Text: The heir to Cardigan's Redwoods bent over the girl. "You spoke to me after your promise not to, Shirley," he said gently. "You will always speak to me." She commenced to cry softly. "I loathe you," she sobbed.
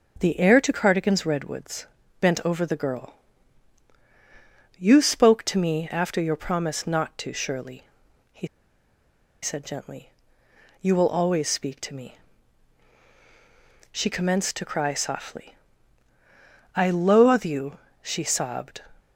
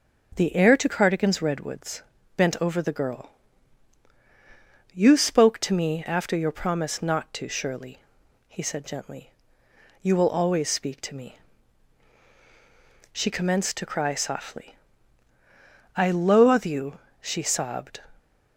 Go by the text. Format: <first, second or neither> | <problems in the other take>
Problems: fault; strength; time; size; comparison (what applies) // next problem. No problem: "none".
second | pauses between "Redwoods" and "bent"; slight; at 1.8 s; 0.36 s long; slight in the second // pauses between "he" and "said"; noticeable; at 8.4 s; 0.95 s long